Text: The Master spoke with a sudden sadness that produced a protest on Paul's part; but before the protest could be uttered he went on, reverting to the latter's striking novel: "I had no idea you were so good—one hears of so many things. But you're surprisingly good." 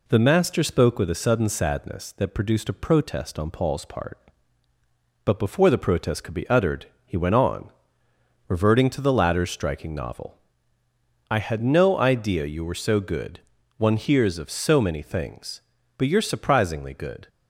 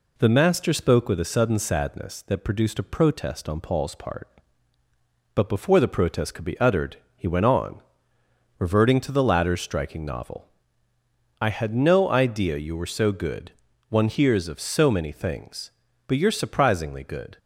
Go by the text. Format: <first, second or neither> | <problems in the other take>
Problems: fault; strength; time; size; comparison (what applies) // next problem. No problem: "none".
neither | pauses between "uttered" and "he"; slight; the same in both